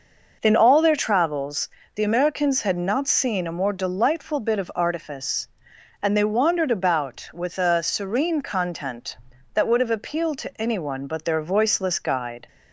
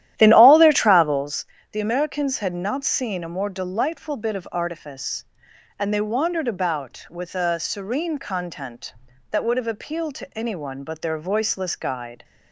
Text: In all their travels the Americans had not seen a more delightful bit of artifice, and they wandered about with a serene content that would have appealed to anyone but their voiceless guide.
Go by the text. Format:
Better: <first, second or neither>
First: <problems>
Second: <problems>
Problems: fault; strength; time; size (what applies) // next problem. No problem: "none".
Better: first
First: pauses between "travels" and "the"; slight; at 1.6 s; 0.28 s long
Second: starts louder than the rest; strong; until 1.4 s; 12.5 dB // pauses between "travels" and "the"; slight; at 1.4 s; 0.28 s long